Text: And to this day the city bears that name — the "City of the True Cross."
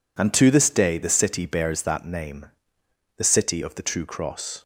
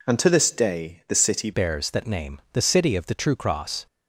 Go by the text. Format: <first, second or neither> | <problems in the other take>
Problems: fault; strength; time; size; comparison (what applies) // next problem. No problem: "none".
first | changes voice at "bears"; from 1.5 s on; 2.3 s long